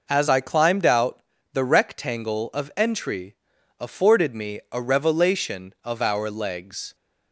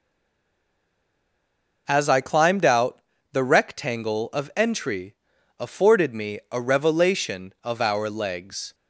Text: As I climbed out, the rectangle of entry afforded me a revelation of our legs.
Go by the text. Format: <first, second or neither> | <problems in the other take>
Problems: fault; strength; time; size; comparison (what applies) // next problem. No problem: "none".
first | stays silent before the first word; noticeable; until 1.8 s; 1.8 s long // pauses between "entry" and "afforded"; at 5.1 s; 0.44 s long; also in the first